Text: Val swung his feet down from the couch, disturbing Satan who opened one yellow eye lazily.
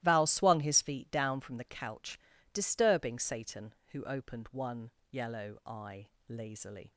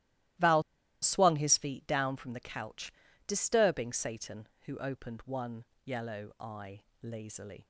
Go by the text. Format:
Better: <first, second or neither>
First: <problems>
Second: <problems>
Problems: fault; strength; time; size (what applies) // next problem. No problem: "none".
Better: first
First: starts louder than the rest; strong; until 1.0 s; 15.5 dB // pauses between "one" and "yellow"; slight; at 4.9 s; 0.20 s long // pauses between "eye" and "lazily"; slight; at 6.0 s; 0.20 s long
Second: starts louder than the rest; strong; until 1.7 s; 15.5 dB // pauses between "Val" and "swung"; at 0.6 s; 0.40 s long // pauses between "one" and "yellow"; slight; at 5.6 s; 0.20 s long // pauses between "eye" and "lazily"; slight; at 6.8 s; 0.20 s long